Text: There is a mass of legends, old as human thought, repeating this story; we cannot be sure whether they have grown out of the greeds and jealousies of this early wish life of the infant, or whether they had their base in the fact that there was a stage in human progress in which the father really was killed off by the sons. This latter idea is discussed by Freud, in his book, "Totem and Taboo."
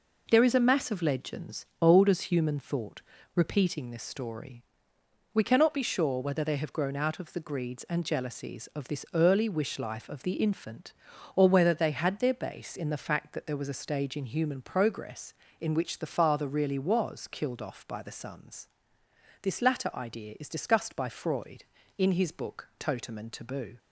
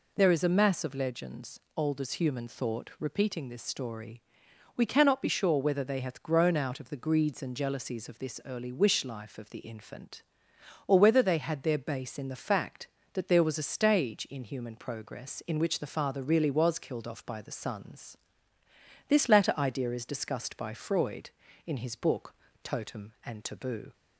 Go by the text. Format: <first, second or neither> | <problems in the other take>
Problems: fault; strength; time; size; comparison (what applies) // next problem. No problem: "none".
first | says "hath" for "have"; at 6.0 s